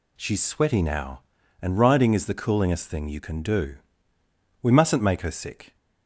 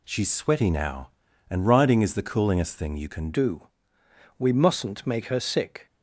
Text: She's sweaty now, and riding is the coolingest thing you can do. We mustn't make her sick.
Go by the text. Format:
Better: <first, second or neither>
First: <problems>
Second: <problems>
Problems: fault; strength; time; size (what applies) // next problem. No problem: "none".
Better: first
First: none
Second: changes voice at "do"; from 3.3 s on; 2.5 s long